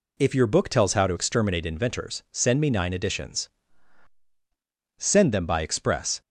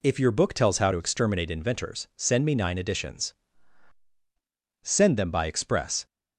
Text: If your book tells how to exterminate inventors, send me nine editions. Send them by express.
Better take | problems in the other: neither | none

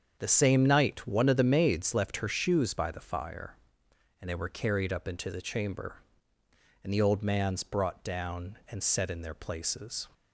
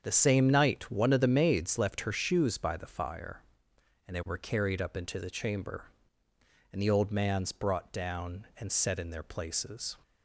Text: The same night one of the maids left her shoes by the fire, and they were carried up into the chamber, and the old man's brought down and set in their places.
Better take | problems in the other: neither | starts louder than the rest; strong; the same in both

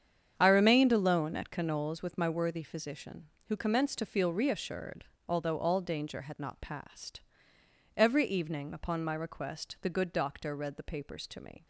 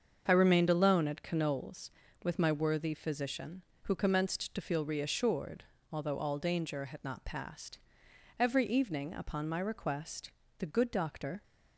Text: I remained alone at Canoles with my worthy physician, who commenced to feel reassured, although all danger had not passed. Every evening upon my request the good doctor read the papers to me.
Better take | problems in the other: first | starts louder than the rest; until 1.2 s; 7 dB; strong in the first // pauses between "request" and "the"; slight; at 10.3 s; 0.28 s long // stops before "read the papers to me"; at 11.4 s

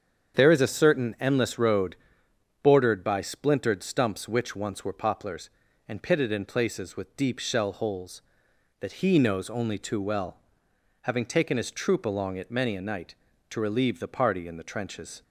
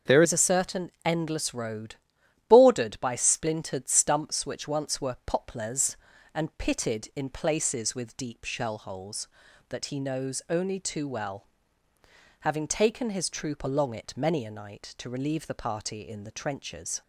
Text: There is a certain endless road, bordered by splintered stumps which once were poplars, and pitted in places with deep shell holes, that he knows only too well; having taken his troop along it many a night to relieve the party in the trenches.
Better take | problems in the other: first | starts louder than the rest; until 1.2 s; 6.5 dB; strong in the first // changes voice at "is"; from 0.2 s on; 16.8 s long

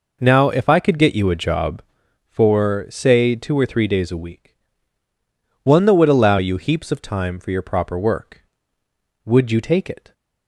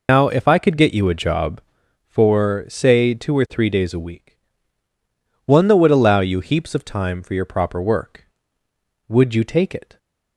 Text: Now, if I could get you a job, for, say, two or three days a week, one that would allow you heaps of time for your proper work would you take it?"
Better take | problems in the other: first | loses the start of "Now"; at 0.0 s; 110 ms

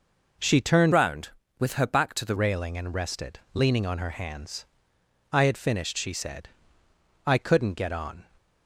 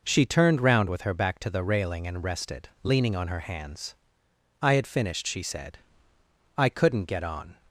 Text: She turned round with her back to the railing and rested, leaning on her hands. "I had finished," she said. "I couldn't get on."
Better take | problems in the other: second | changes voice from "round" to "the"; from 0.9 to 2.3 s; 1.4 s long

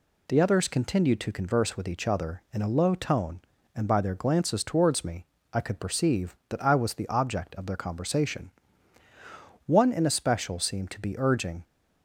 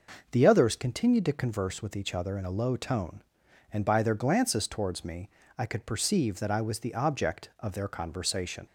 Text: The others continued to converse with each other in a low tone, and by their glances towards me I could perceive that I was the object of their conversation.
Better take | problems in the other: second | pauses between "me" and "I"; slight; at 5.2 s; 0.26 s long; slight in the second // goes on to say "One in especial seemed to be urging"; strong; from 9.6 s on; 1.9 s long

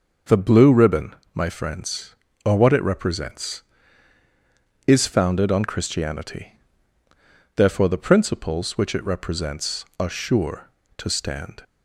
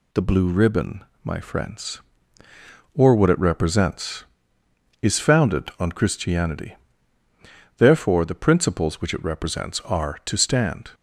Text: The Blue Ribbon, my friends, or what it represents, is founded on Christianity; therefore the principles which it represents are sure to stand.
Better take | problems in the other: first | skips "sure"; at 10.2 s

